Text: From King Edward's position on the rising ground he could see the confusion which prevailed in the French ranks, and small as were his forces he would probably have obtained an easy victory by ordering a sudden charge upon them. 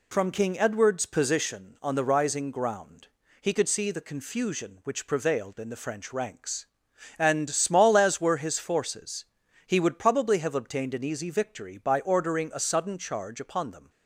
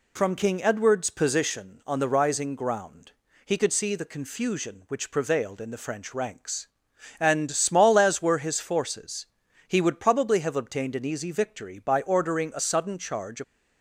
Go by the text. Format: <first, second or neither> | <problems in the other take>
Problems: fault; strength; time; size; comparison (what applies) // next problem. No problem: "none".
first | pauses between "ground" and "he"; slight; at 3.1 s; 0.34 s long; slight in the first // pauses between "forces" and "he"; at 9.2 s; 0.42 s long; also in the first // stops before "upon them"; at 13.4 s